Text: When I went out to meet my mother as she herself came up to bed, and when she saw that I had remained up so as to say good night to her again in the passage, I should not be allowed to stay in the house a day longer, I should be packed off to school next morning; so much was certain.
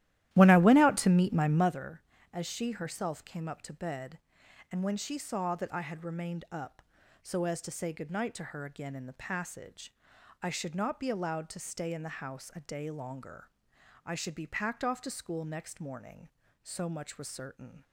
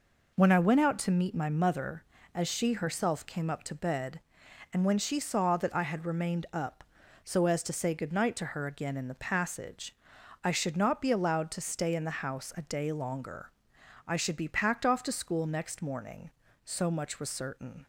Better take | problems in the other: second | starts louder than the rest; strong; until 1.8 s; 14 dB

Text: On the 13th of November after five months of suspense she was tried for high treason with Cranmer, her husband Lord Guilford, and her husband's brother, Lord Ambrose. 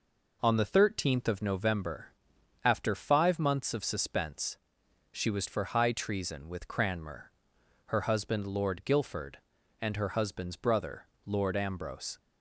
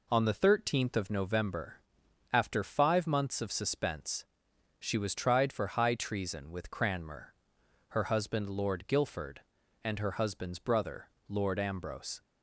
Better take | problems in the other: second | pauses between "November" and "after"; noticeable; at 2.1 s; 0.52 s long; noticeable in the second // pauses between "suspense" and "she"; noticeable; at 4.5 s; 0.56 s long; noticeable in the second // skips "tried"; at 5.4 s

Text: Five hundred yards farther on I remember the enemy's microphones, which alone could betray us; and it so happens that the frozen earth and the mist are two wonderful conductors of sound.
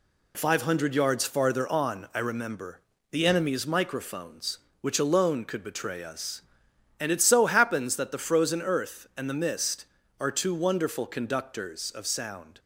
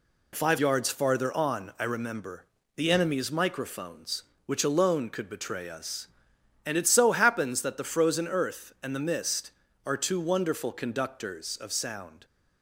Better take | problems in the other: first | skips "hundred"; at 0.5 s // pauses between "remember" and "the"; slight; at 2.4 s; 0.28 s long; slight in the first

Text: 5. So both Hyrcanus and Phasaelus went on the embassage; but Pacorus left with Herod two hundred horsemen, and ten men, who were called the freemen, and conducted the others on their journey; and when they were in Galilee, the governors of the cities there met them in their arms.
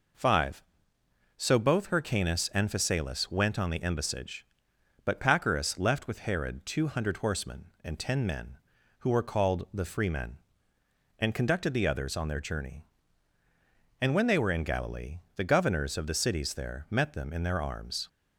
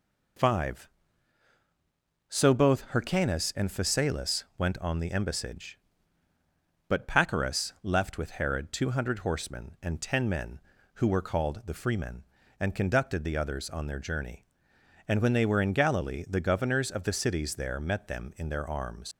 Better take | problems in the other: first | leaves "arms" unfinished; at 19.1 s; 100 ms

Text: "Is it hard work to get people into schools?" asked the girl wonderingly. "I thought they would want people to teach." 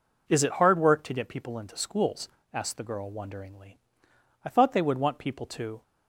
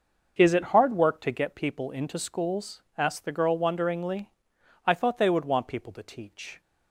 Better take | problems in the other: second | stops before "teach"; at 5.8 s

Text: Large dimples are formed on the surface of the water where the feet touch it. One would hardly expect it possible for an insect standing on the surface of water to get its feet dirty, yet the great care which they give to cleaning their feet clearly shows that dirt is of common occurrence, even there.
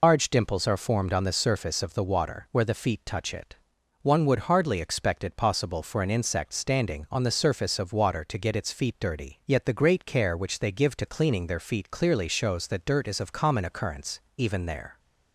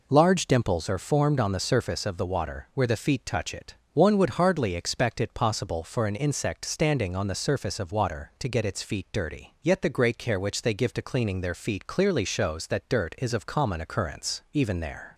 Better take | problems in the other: second | loses the start of "Large"; at 0.0 s; 105 ms

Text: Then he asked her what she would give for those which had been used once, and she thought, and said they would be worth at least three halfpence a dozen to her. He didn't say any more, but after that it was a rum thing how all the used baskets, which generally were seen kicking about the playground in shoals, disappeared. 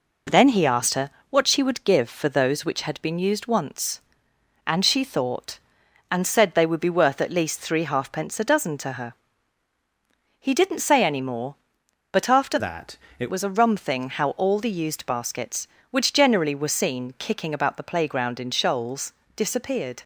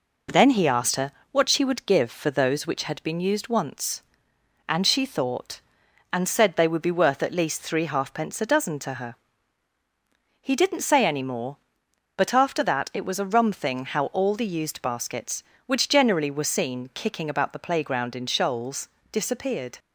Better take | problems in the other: second | pauses between "her" and "what"; slight; at 1.0 s; 0.20 s long; slight in the second // changes voice from "that" to "it"; from 12.5 to 13.3 s; 0.8 s long // pauses between "that" and "it"; slight; at 12.9 s; 0.22 s long

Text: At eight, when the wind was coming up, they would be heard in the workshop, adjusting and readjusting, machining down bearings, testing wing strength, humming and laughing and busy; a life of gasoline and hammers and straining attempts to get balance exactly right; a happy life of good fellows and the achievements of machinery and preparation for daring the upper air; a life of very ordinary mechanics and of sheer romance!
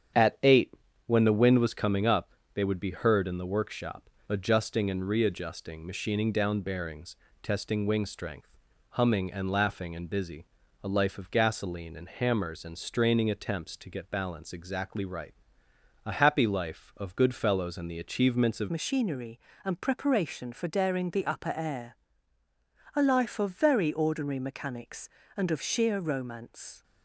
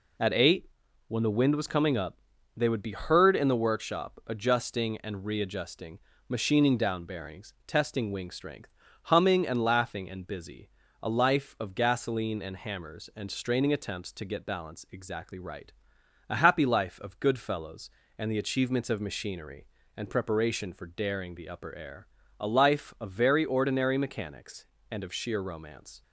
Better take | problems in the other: second | starts louder than the rest; strong; until 1.5 s; 9 dB // changes voice at "machinery"; from 18.7 s on; 8.1 s long

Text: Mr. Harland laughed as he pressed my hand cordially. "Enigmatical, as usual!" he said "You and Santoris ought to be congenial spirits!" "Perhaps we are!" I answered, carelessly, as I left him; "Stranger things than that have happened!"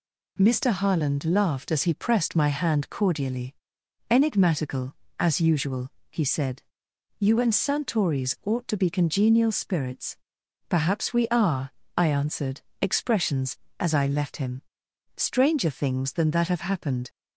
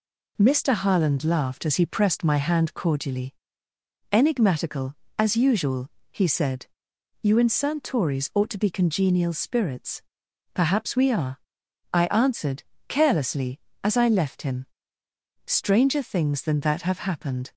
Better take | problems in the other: second | pauses between "said" and "You"; noticeable; at 6.6 s; 0.56 s long; noticeable in the second // says "expressions" for "carelessly"; at 12.8 s

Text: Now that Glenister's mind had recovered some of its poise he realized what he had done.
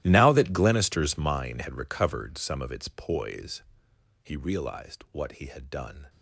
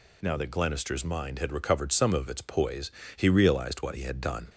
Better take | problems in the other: second | gets quieter; strong; throughout; 19.5 dB // pauses between "poise" and "he"; noticeable; at 3.6 s; 0.60 s long; slight in the second

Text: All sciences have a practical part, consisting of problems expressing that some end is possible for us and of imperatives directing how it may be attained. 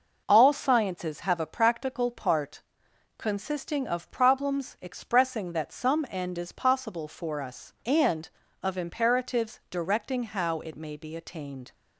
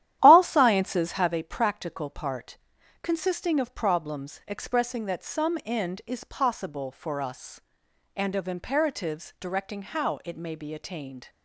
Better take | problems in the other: first | starts louder than the rest; strong; until 1.3 s; 12 dB

